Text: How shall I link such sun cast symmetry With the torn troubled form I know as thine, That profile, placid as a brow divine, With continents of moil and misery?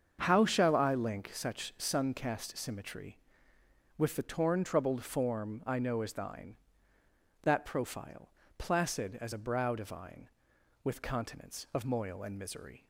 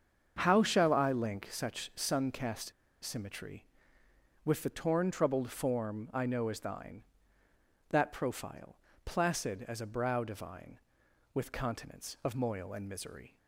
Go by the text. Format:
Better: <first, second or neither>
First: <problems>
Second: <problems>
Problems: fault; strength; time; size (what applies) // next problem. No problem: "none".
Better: first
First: starts louder than the rest; until 1.2 s; 7 dB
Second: starts louder than the rest; until 1.4 s; 7 dB // pauses between "cast" and "symmetry"; slight; at 2.7 s; 0.32 s long